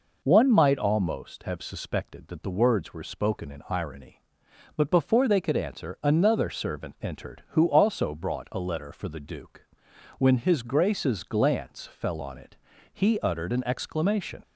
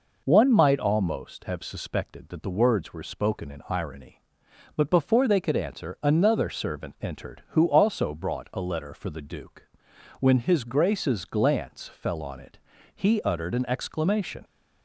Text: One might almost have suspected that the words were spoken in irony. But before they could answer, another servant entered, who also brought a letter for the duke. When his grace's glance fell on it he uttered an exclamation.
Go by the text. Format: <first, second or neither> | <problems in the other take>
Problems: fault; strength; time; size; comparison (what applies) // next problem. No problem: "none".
neither | pauses between "it" and "he"; slight; the same in both